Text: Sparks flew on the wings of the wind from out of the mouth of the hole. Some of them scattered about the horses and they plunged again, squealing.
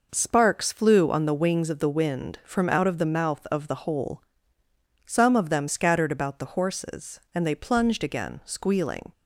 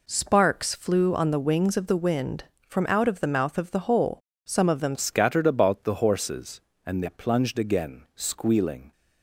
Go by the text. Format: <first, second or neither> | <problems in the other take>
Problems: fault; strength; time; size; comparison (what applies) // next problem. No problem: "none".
first | changes voice at "scattered"; from 4.9 s on; 4.0 s long